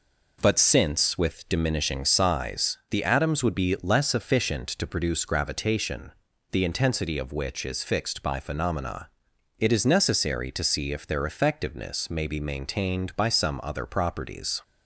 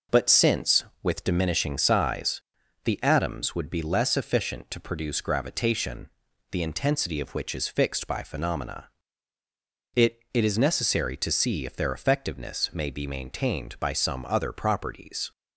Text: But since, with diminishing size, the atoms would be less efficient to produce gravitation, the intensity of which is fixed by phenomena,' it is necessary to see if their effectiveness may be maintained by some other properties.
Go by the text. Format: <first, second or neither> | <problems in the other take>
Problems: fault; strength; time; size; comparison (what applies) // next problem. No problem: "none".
first | says "it" twice; at 10.3 s